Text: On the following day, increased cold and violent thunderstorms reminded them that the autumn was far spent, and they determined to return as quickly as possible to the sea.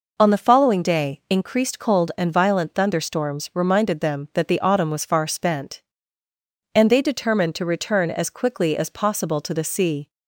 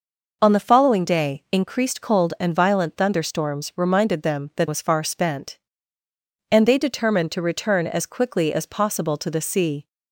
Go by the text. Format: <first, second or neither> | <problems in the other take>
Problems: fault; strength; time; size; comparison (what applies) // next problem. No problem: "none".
first | skips "the autumn"; at 4.6 s